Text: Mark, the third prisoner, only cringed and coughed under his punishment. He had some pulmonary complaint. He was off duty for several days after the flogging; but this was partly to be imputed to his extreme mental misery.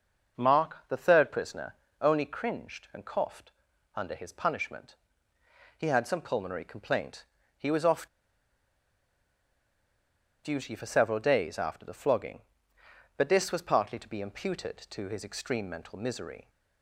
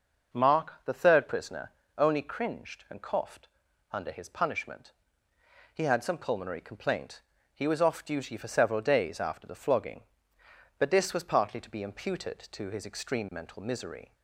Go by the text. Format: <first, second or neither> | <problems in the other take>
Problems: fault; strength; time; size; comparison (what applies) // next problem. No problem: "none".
second | pauses between "coughed" and "under"; at 3.5 s; 0.44 s long; also in the second // pauses between "off" and "duty"; strong; at 8.0 s; 2.3 s long